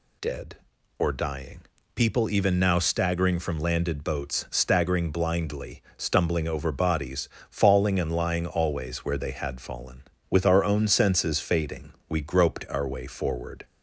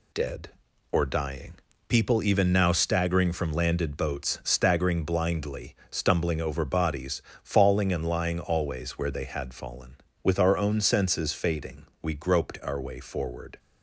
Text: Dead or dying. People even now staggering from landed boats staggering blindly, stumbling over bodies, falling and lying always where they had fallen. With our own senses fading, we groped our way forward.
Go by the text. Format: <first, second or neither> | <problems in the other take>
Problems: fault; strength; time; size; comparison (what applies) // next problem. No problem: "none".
first | gets quieter; noticeable; throughout; 5 dB